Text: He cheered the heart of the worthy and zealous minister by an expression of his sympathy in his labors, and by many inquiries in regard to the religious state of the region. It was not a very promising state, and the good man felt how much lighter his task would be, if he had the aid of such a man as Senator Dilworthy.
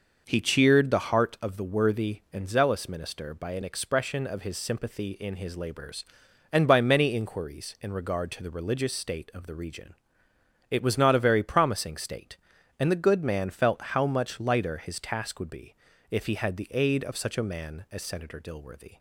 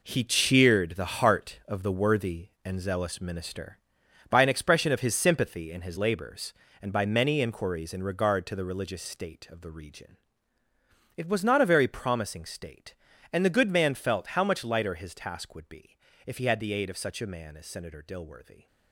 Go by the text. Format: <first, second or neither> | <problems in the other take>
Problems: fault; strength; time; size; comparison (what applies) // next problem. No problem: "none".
first | gets quieter; strong; throughout; 9.5 dB